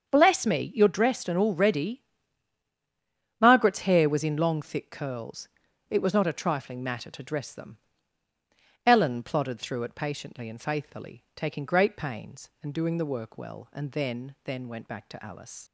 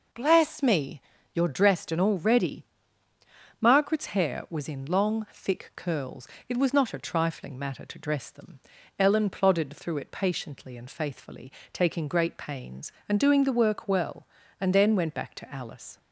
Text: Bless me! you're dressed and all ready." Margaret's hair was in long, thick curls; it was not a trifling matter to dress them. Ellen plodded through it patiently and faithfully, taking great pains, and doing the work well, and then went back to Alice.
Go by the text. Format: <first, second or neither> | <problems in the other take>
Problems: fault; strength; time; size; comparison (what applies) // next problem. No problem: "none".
second | starts louder than the rest; strong; until 1.1 s; 7 dB // says "then" twice; at 14.4 s